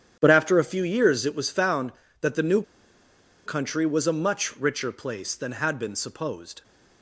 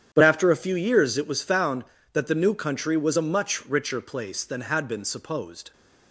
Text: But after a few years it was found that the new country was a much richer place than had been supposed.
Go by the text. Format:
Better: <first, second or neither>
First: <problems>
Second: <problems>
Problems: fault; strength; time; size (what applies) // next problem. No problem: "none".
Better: second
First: starts louder than the rest; strong; until 1.2 s; 9.5 dB // pauses between "new" and "country"; noticeable; at 2.6 s; 0.84 s long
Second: starts louder than the rest; strong; until 1.1 s; 9.5 dB